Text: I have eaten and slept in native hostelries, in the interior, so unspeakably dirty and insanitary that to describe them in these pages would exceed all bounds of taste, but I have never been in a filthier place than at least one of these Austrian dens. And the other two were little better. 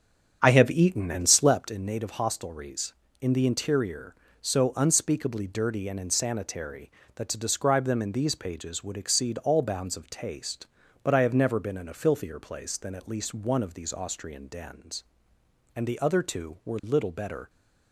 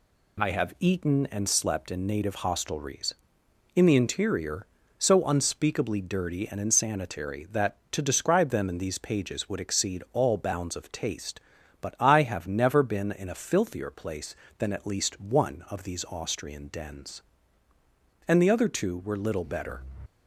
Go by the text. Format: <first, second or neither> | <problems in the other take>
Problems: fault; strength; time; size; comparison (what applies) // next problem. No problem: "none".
second | starts louder than the rest; strong; until 1.8 s; 7.5 dB